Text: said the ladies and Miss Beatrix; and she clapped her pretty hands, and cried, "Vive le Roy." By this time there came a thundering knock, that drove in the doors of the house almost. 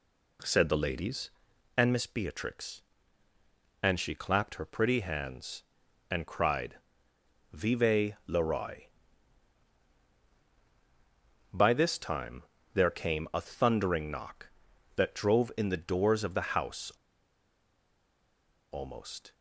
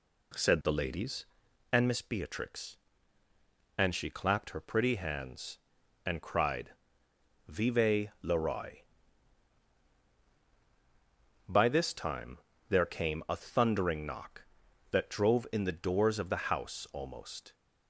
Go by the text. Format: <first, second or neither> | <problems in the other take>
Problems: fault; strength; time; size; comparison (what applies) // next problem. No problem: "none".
second | pauses between "time" and "there"; slight; at 12.4 s; 0.30 s long; slight in the second // pauses between "house" and "almost"; strong; at 16.9 s; 1.8 s long